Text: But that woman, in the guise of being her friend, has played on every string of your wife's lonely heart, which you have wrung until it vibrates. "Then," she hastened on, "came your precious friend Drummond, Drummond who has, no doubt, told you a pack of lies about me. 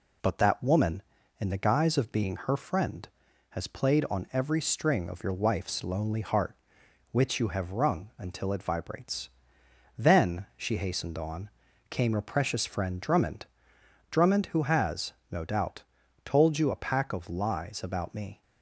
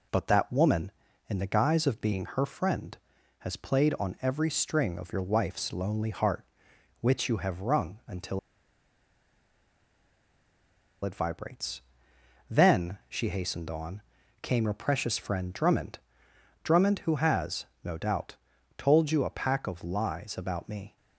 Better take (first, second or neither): first